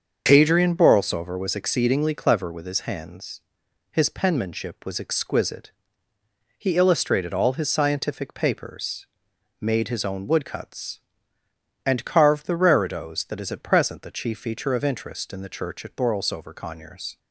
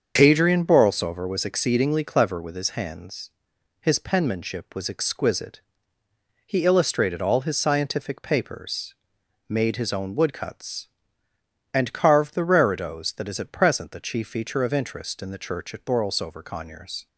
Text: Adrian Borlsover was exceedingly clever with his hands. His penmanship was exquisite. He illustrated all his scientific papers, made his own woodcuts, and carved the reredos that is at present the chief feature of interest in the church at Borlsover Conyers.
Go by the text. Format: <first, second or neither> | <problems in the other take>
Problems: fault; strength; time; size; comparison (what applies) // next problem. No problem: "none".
neither | starts louder than the rest; the same in both